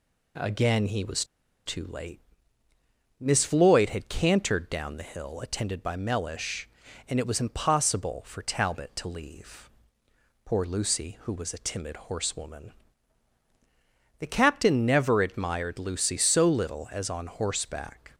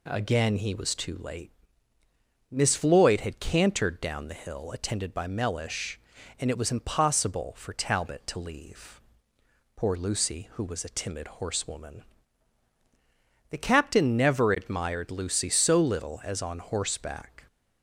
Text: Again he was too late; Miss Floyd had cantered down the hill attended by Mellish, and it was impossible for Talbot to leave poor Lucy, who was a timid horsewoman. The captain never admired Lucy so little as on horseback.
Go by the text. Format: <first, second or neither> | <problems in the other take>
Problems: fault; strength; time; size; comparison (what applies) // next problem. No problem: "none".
second | pauses between "was" and "too"; at 1.2 s; 0.41 s long // pauses between "leave" and "poor"; noticeable; at 9.6 s; 0.74 s long; noticeable in the second